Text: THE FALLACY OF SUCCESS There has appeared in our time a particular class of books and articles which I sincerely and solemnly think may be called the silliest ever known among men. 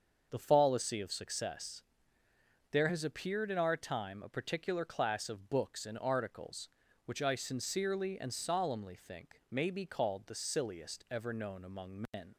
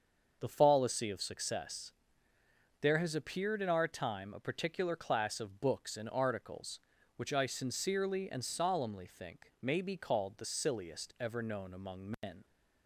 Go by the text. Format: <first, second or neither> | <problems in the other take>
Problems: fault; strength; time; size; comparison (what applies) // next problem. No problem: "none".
neither | starts louder than the rest; the same in both // pauses between "SUCCESS" and "There"; noticeable; the same in both